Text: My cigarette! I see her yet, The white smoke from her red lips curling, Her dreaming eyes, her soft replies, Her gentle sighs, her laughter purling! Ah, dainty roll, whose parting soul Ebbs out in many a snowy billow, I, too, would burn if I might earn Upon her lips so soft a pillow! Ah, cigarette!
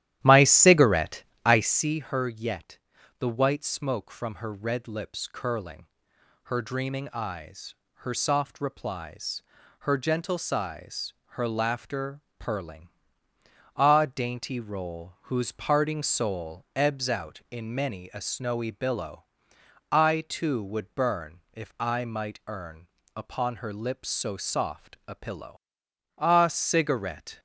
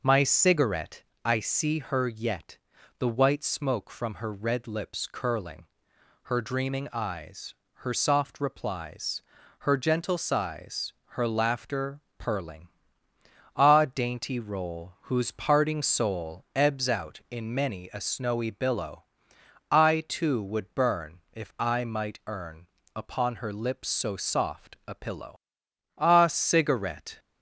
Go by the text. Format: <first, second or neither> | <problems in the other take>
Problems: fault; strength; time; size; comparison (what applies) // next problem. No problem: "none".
second | starts louder than the rest; strong; until 1.9 s; 13 dB // pauses between "laughter" and "purling"; slight; at 12.2 s; 0.16 s long; slight in the second // pauses between "earn" and "Upon"; slight; at 22.8 s; 0.30 s long; slight in the second